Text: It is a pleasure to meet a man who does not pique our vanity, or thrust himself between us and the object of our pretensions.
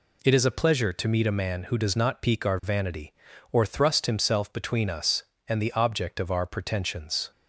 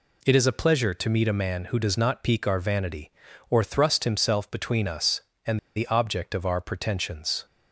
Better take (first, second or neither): first